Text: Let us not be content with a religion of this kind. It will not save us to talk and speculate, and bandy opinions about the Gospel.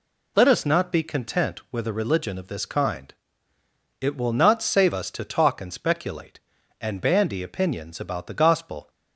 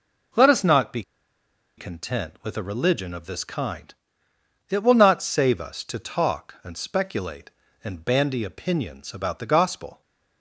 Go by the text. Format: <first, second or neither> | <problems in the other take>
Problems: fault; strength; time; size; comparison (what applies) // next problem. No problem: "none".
first | pauses between "be" and "content"; noticeable; at 1.0 s; 0.75 s long